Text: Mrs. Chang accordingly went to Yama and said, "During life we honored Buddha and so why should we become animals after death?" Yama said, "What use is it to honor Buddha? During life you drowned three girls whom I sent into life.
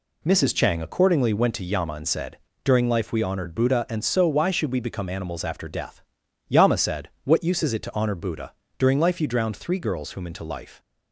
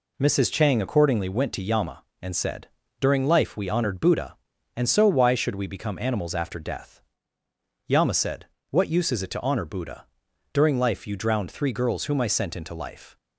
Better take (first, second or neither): second